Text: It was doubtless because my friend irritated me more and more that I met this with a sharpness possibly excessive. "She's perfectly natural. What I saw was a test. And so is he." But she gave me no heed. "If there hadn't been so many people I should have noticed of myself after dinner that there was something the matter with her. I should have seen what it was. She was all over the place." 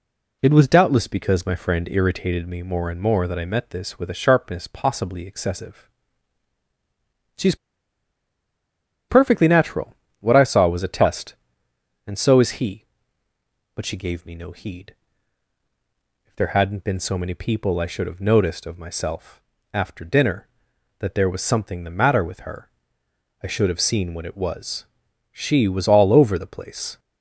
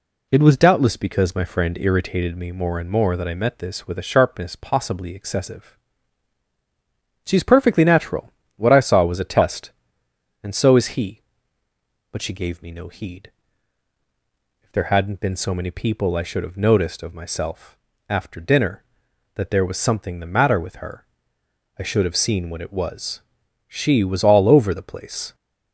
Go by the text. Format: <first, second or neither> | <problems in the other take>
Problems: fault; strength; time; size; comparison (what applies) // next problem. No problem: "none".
second | pauses between "She's" and "perfectly"; strong; at 7.5 s; 1.5 s long // pauses between "myself" and "after"; slight; at 19.4 s; 0.32 s long; slight in the second